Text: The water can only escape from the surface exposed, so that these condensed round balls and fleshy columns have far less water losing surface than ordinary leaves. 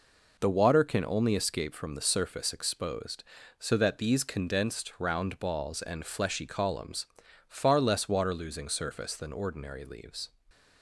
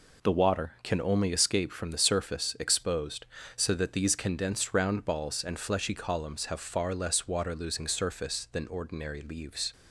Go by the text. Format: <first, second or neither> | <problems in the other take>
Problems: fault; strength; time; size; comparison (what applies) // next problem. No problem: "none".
second | skips "have"; at 7.2 s